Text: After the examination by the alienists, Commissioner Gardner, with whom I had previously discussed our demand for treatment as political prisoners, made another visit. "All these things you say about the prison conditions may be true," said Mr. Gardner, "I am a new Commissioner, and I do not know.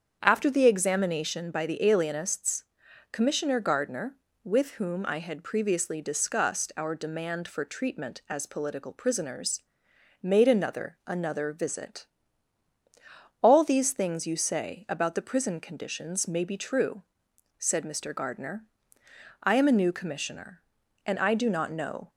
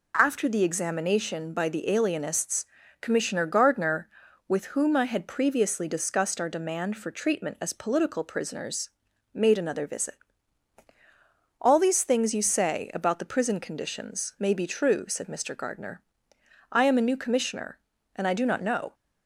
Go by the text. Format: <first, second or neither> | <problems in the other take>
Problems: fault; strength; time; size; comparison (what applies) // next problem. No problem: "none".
second | starts louder than the rest; strong; until 1.2 s; 7.5 dB // says "another" twice; at 11.0 s